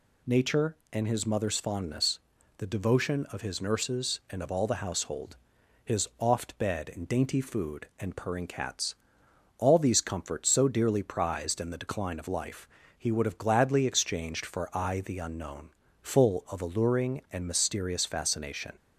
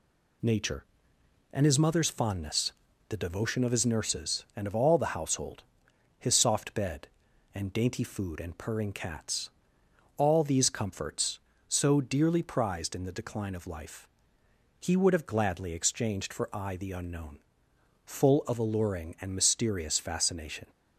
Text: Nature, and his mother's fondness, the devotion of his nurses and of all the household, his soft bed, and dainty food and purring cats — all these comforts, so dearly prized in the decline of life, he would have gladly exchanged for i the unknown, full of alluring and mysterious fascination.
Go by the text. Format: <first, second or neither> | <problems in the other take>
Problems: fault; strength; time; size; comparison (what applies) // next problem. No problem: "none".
second | says "oft" for "soft"; at 6.1 s